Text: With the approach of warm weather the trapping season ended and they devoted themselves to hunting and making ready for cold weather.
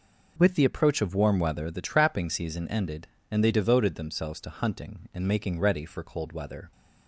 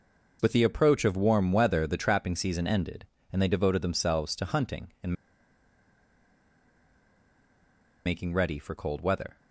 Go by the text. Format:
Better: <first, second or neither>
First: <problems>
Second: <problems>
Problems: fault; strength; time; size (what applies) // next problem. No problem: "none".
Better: first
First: none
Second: pauses between "and" and "making"; strong; at 5.1 s; 2.9 s long